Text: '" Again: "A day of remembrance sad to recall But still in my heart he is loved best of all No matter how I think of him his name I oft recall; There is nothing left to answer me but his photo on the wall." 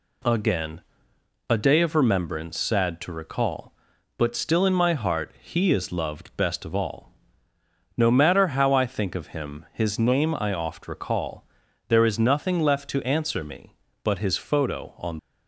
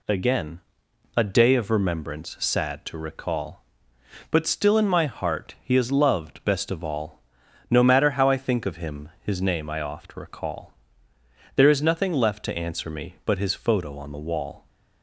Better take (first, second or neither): second